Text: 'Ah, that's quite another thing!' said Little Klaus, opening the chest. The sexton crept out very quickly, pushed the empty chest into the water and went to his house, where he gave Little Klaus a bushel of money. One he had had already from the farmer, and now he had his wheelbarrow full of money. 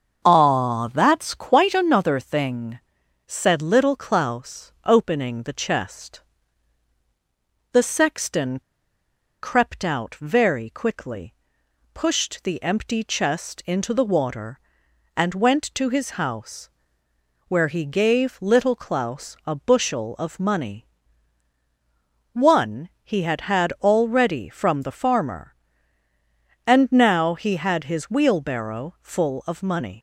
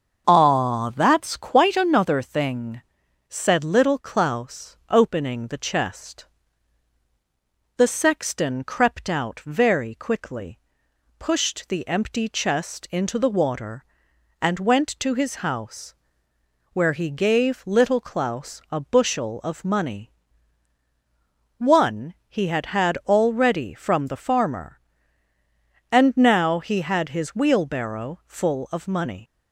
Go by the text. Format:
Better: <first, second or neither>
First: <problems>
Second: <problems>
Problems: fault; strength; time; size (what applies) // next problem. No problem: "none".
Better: second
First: starts louder than the rest; until 1.2 s; 6.5 dB // pauses between "sexton" and "crept"; noticeable; at 8.6 s; 0.82 s long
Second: starts louder than the rest; until 1.2 s; 6.5 dB